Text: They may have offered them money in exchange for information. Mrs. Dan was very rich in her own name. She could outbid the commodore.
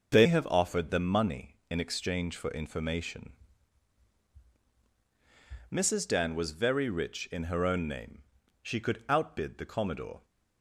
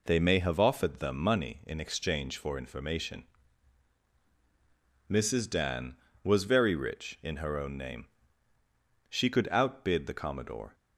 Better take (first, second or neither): second